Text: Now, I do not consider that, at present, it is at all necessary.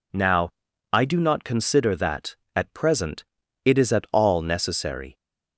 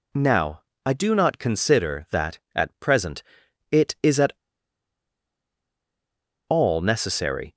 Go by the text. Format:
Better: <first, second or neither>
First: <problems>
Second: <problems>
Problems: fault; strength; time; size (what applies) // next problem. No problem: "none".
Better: first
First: none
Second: pauses between "at" and "all"; strong; at 4.3 s; 2.1 s long